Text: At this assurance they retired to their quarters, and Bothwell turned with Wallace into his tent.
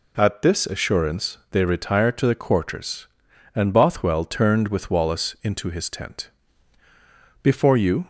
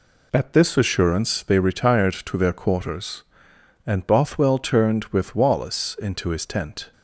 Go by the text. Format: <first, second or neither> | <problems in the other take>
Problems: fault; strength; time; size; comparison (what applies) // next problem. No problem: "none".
second | goes on to say "Before you"; noticeable; from 7.4 s on; 0.64 s long